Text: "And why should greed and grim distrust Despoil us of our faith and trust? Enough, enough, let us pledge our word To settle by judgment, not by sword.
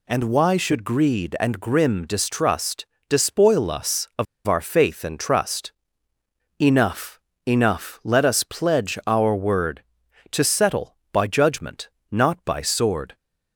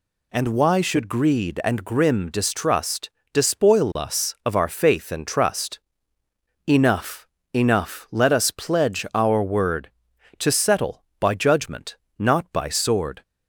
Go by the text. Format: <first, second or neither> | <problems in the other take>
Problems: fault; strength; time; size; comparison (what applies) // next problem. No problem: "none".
second | pauses between "distrust" and "Despoil"; slight; at 2.8 s; 0.24 s long; slight in the second // pauses between "of" and "our"; slight; at 4.2 s; 0.21 s long